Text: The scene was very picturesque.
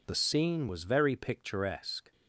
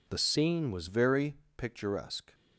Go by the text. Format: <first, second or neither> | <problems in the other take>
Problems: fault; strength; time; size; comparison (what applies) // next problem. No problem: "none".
first | changes voice at "very"; from 0.8 s on; 1.5 s long // pauses between "very" and "picturesque"; slight; at 1.3 s; 0.24 s long